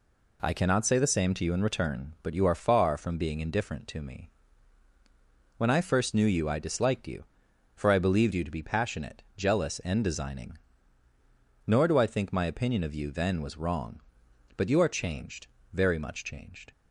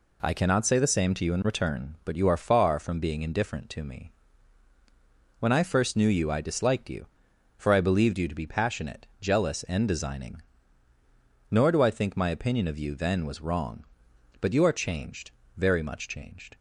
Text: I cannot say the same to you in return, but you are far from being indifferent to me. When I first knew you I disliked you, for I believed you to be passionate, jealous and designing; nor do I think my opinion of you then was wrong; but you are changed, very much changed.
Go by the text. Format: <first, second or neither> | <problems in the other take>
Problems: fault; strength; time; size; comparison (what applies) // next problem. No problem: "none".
neither | none